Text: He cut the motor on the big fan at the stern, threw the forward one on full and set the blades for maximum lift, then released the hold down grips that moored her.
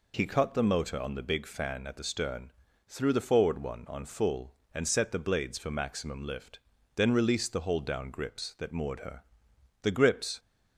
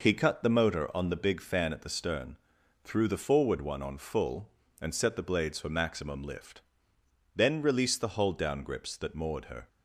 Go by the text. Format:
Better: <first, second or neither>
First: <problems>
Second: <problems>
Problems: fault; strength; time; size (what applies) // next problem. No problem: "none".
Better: second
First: goes on to say "The grips"; from 9.8 s on; 0.56 s long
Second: none